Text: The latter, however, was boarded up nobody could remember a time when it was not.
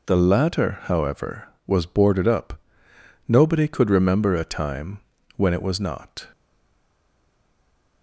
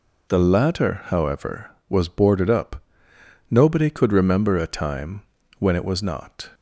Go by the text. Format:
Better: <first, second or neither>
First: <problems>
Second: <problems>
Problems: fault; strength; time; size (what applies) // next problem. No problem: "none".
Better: second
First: pauses between "up" and "nobody"; noticeable; at 2.5 s; 0.68 s long // pauses between "time" and "when"; slight; at 4.9 s; 0.36 s long // stays silent after the last word; noticeable; from 6.3 s on; 1.7 s long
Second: pauses between "up" and "nobody"; noticeable; at 2.8 s; 0.68 s long // pauses between "time" and "when"; slight; at 5.2 s; 0.36 s long